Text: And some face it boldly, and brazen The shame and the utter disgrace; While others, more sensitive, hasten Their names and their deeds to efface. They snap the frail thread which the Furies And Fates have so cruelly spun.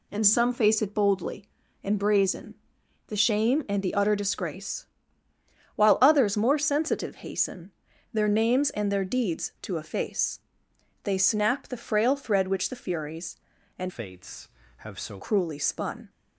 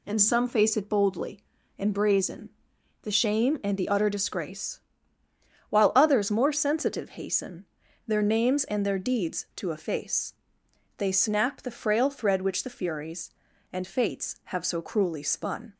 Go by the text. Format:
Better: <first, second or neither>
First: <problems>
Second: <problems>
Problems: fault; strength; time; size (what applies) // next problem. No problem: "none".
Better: second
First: pauses between "brazen" and "The"; noticeable; at 2.5 s; 0.52 s long // pauses between "hasten" and "Their"; at 7.7 s; 0.42 s long // changes voice from "Fates" to "so"; from 13.8 to 15.1 s; 1.3 s long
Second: pauses between "brazen" and "The"; noticeable; at 2.4 s; 0.52 s long // pauses between "hasten" and "Their"; at 7.6 s; 0.42 s long